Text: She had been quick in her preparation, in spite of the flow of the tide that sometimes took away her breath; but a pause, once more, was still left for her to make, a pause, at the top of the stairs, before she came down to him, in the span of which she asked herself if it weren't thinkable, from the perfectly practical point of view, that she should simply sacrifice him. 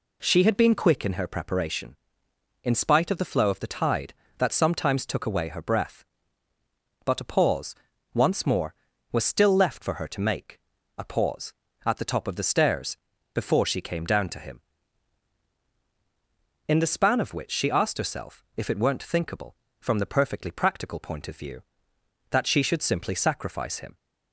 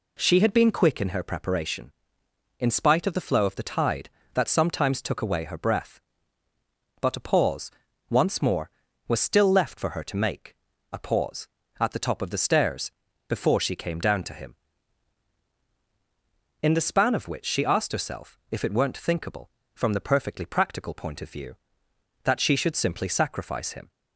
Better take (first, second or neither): neither